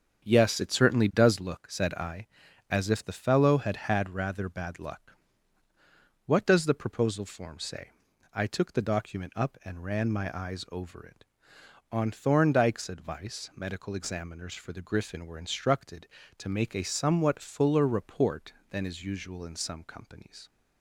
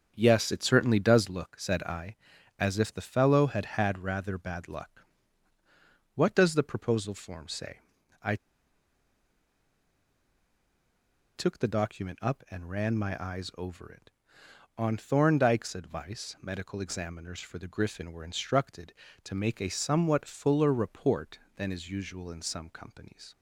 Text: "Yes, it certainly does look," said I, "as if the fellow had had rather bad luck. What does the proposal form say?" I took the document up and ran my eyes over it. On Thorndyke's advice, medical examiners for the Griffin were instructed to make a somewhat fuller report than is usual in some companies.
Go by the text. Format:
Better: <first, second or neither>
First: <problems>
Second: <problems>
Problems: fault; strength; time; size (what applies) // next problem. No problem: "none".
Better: first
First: starts louder than the rest; strong; until 1.3 s; 7.5 dB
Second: starts louder than the rest; strong; until 1.1 s; 7.5 dB // pauses between "I" and "took"; strong; at 8.3 s; 2.9 s long